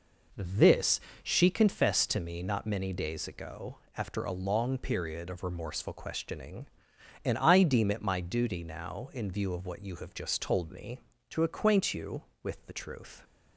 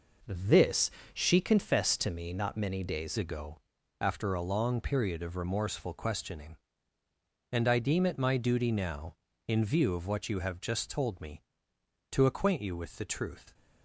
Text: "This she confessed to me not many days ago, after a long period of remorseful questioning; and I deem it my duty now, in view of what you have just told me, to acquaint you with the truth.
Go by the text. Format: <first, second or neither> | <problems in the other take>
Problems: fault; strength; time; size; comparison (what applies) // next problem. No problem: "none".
first | pauses between "This" and "she"; slight; at 0.9 s; 0.22 s long; slight in the first // changes voice at "ago"; from 3.1 s on; 10.4 s long